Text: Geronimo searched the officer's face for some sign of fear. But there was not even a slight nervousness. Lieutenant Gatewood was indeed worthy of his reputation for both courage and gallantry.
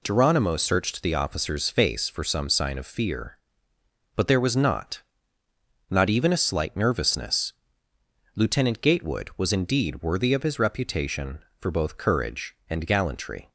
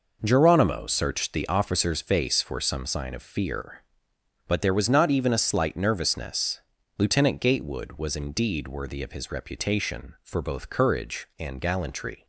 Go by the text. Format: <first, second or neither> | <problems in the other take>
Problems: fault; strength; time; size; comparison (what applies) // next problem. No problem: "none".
second | says "not" twice; at 5.9 s